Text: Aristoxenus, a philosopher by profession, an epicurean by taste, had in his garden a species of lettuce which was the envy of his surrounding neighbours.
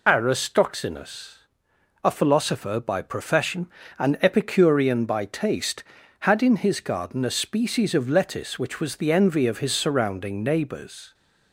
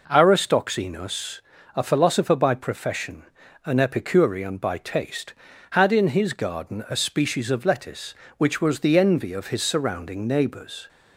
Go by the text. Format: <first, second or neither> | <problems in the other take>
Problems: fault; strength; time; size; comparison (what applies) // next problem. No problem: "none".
second | loses the start of "Aristoxenus"; at 0.0 s; 60 ms